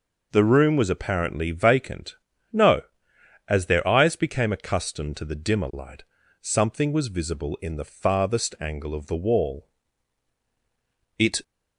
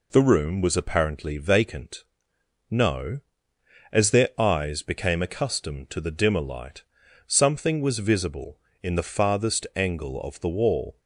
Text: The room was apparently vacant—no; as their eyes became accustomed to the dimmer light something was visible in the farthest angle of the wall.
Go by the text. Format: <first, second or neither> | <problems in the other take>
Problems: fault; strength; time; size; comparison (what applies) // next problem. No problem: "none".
second | pauses between "light" and "something"; slight; at 6.0 s; 0.36 s long; noticeable in the second // goes on to say "It"; slight; from 11.1 s on; 0.24 s long